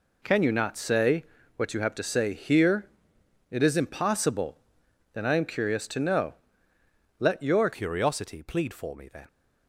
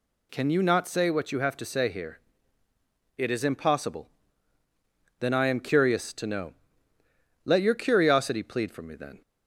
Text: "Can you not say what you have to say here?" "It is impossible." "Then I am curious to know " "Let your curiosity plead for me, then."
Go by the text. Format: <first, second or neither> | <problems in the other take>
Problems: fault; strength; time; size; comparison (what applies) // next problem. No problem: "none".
second | pauses between "say" and "what"; slight; at 1.2 s; 0.32 s long // changes voice at "curiosity"; from 7.7 s on; 1.5 s long